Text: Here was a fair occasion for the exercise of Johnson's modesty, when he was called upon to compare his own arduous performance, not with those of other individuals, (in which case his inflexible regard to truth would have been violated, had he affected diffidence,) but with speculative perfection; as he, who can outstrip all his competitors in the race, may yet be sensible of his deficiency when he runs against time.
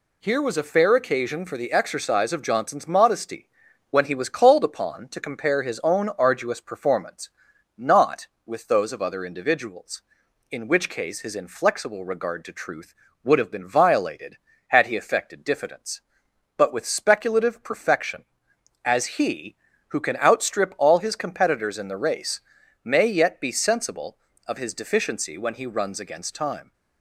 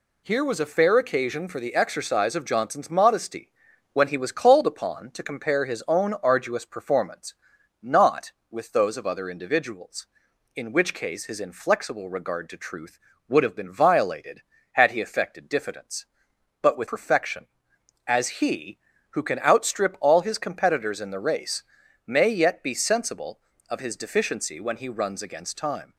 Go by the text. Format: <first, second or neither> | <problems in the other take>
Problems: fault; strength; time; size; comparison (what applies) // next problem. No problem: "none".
first | skips "speculative"; at 16.8 s